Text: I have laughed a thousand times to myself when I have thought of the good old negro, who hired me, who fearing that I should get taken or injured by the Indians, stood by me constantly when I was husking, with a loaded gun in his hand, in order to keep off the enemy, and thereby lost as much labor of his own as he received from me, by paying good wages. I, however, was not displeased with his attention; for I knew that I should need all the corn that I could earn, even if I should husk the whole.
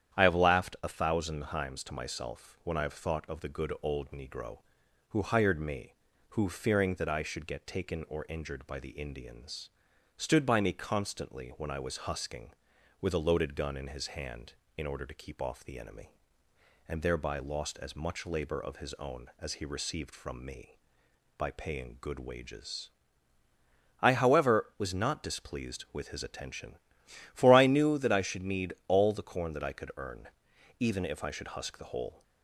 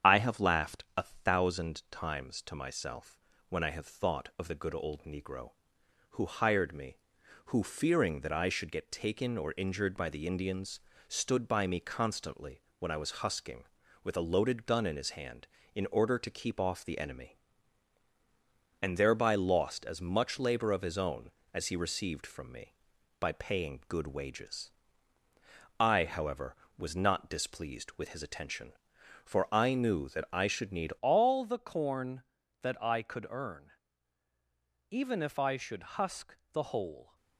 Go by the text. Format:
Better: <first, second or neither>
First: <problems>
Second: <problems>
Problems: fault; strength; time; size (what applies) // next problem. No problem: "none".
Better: first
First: starts louder than the rest; strong; until 1.2 s; 9.5 dB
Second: starts louder than the rest; strong; until 1.1 s; 8.5 dB // pauses between "myself" and "when"; slight; at 3.1 s; 0.30 s long // pauses between "constantly" and "when"; slight; at 12.6 s; 0.18 s long // changes voice at "all"; from 31.0 s on; 6.1 s long // pauses between "should" and "husk"; slight; at 35.8 s; 0.16 s long // pauses between "husk" and "the"; slight; at 36.3 s; 0.16 s long